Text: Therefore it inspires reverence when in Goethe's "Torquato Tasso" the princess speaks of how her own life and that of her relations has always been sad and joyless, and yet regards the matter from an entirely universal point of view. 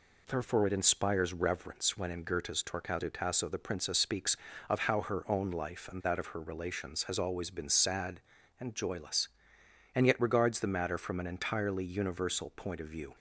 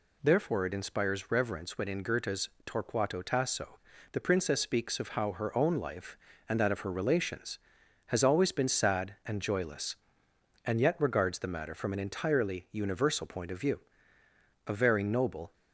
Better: first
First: none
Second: pauses between "Goethe's" and "Torquato"; slight; at 2.4 s; 0.16 s long // pauses between "Tasso" and "the"; slight; at 3.7 s; 0.35 s long // goes on to say "A very noble"; noticeable; from 14.6 s on; 0.86 s long

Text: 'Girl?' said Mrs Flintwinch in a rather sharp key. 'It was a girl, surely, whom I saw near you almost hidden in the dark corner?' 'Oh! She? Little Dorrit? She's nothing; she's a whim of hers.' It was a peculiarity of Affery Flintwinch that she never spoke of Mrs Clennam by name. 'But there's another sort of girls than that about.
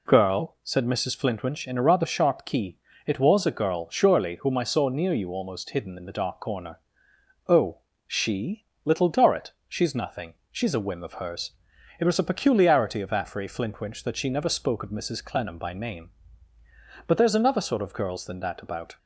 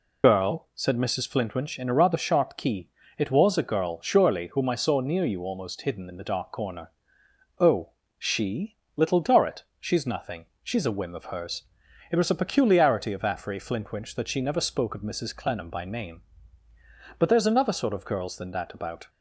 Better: first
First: none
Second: loses the start of "Girl"; at 0.2 s; 50 ms

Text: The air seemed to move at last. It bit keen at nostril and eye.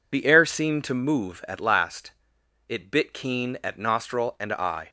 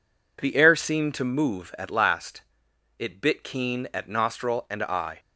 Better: second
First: loses the start of "The"; at 0.1 s; 45 ms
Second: none

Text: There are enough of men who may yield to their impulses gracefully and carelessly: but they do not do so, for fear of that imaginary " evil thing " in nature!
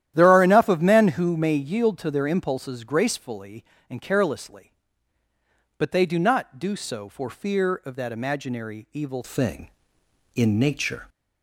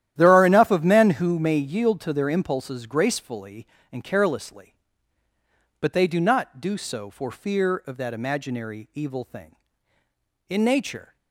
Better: second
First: starts louder than the rest; strong; until 1.1 s; 11.5 dB // changes voice at "thing"; from 9.2 s on; 1.8 s long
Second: starts louder than the rest; strong; until 1.1 s; 11.5 dB

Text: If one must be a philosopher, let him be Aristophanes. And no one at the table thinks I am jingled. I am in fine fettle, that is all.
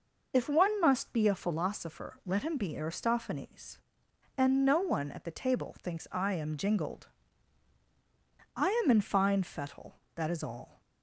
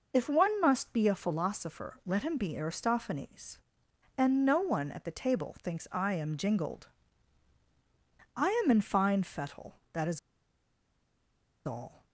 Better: first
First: pauses between "I" and "am"; slight; at 8.6 s; 0.16 s long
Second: pauses between "I" and "am"; slight; at 8.4 s; 0.16 s long // pauses between "is" and "all"; strong; at 10.1 s; 1.4 s long

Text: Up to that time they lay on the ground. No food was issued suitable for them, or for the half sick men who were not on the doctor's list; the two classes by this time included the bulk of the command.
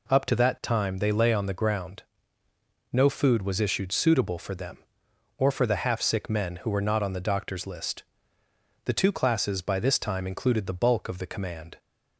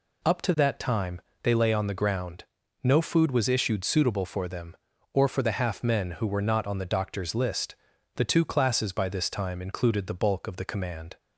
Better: first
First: none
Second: pauses between "time" and "they"; slight; at 1.1 s; 0.22 s long // skips "sick"; at 5.8 s

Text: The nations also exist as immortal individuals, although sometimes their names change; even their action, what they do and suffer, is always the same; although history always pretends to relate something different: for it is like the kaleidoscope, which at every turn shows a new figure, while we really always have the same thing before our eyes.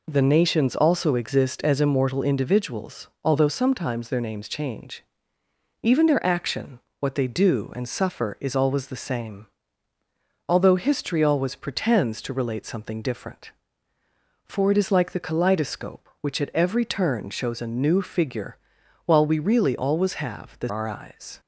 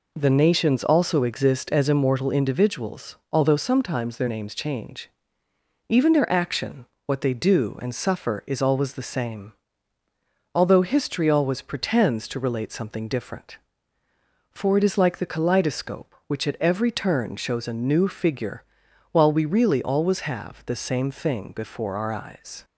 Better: second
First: skips "same thing before"; at 20.6 s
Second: none

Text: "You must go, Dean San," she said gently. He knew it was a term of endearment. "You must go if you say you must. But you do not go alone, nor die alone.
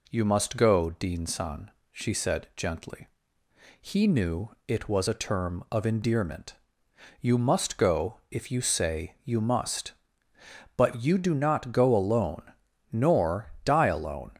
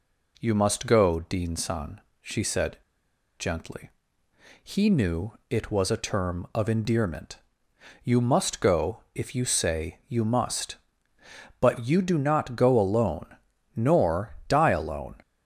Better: first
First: none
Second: pauses between "said" and "gently"; noticeable; at 2.7 s; 0.60 s long

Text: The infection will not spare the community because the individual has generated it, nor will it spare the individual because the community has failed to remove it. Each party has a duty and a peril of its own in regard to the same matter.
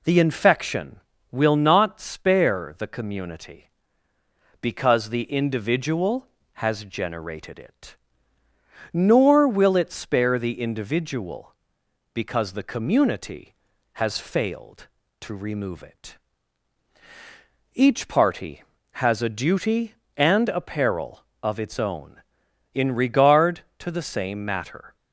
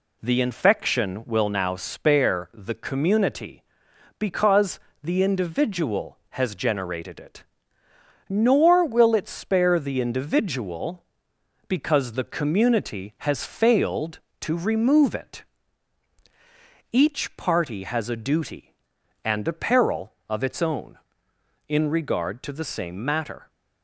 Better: first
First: none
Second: says "now" for "not"; at 1.4 s // pauses between "because" and "the"; slight; at 4.7 s; 0.24 s long

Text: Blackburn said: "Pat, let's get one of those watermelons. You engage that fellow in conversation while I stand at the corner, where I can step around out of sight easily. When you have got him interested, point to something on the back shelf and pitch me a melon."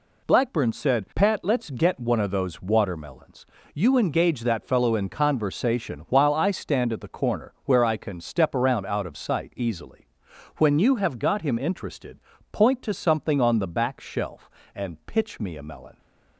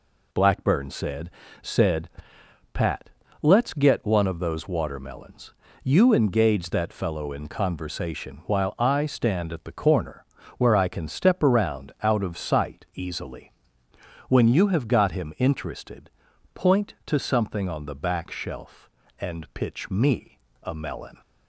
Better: first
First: none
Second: says "said" twice; at 1.6 s // pauses between "me" and "a"; slight; at 20.3 s; 0.26 s long

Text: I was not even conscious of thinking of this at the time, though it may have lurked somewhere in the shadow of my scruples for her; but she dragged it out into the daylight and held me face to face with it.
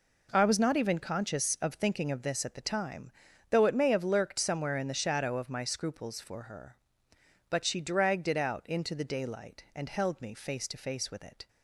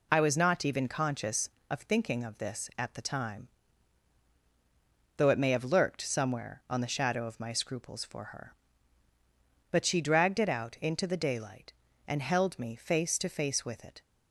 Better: first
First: none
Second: says "on" for "in"; at 6.6 s

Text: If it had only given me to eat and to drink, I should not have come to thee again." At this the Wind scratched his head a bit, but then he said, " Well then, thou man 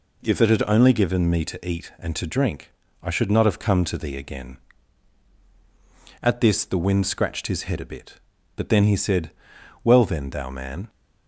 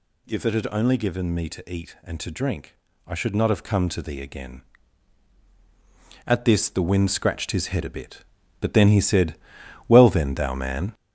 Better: first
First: none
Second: gets louder; noticeable; throughout; 4.5 dB

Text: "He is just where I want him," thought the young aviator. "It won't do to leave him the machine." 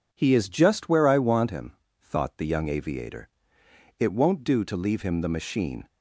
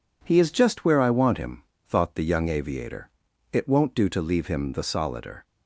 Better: first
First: none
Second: says "solider" for "machine"; at 4.8 s

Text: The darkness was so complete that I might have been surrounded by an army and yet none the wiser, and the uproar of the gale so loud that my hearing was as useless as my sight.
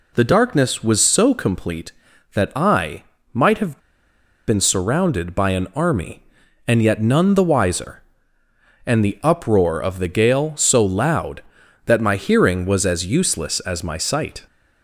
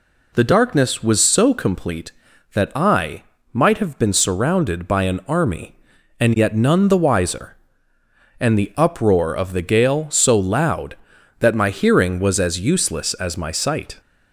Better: second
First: pauses between "I" and "might"; slight; at 3.0 s; 0.30 s long // pauses between "have" and "been"; noticeable; at 3.7 s; 0.68 s long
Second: pauses between "I" and "might"; slight; at 3.2 s; 0.30 s long

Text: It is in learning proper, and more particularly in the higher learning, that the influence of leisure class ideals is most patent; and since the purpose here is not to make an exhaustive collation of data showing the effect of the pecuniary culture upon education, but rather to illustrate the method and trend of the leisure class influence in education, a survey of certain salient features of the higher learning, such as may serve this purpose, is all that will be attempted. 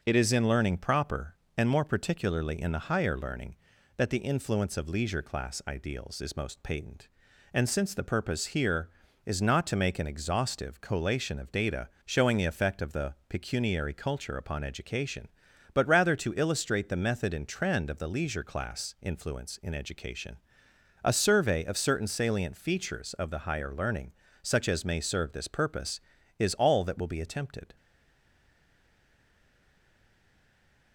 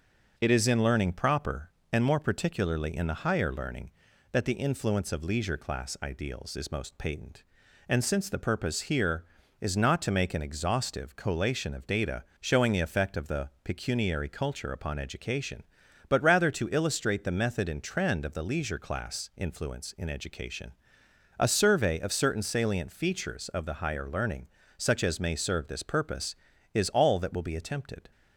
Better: second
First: pauses between "data" and "showing"; slight; at 11.8 s; 0.16 s long // stays silent after the last word; strong; from 27.7 s on; 3.2 s long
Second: pauses between "data" and "showing"; slight; at 12.2 s; 0.16 s long

